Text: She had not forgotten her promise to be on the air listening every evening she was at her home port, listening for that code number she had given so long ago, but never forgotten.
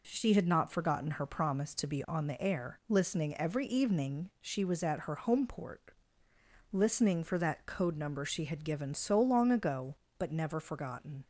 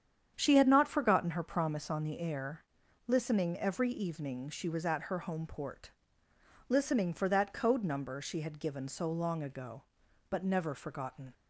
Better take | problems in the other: first | starts louder than the rest; strong; until 1.3 s; 8.5 dB // skips "to be"; at 1.8 s // pauses between "air" and "listening"; at 2.6 s; 0.42 s long

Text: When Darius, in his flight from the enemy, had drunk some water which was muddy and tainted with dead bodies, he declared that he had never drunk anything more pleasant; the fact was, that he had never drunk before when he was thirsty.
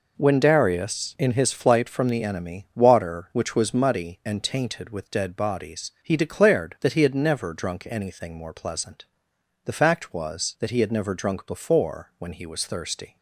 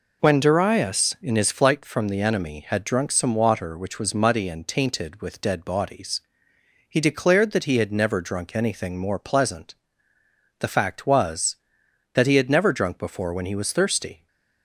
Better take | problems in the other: second | skips "had drunk some"; at 2.7 s

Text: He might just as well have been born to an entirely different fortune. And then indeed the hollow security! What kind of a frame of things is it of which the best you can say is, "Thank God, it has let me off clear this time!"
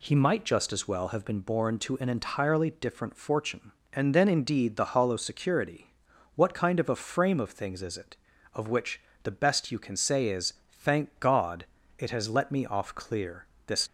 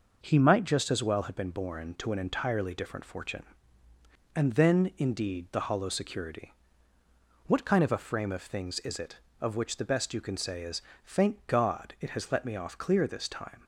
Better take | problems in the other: second | pauses between "which" and "the"; slight; at 8.9 s; 0.22 s long // pauses between "clear" and "this"; slight; at 13.4 s; 0.22 s long // stops before "time"; at 13.8 s

